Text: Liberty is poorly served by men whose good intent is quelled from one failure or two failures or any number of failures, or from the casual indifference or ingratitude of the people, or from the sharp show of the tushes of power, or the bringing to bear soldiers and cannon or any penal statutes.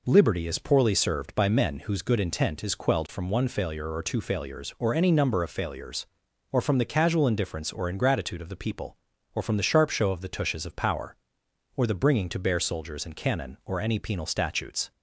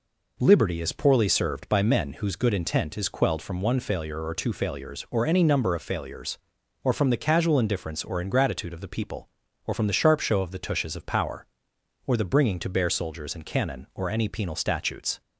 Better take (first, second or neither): neither